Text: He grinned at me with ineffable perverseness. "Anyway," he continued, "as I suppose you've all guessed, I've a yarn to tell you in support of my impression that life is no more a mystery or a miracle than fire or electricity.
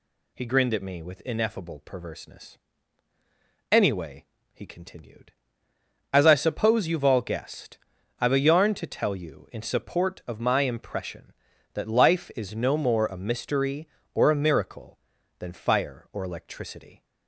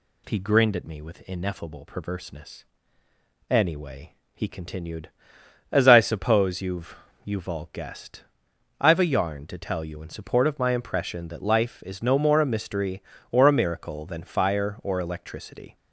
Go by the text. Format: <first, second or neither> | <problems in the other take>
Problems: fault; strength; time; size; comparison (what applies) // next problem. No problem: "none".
first | says "you've" twice; at 7.2 s